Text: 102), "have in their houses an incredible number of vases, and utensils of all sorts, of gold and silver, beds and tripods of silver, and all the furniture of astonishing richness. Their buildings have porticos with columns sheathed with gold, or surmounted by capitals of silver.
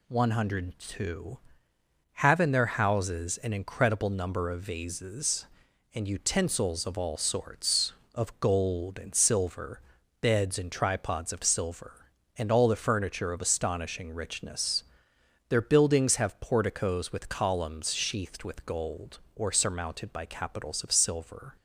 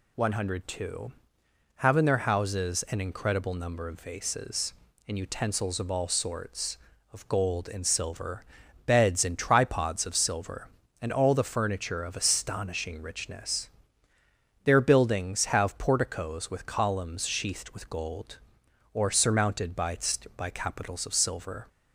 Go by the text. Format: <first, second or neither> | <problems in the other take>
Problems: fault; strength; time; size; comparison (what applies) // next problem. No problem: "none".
first | says "by" twice; at 20.3 s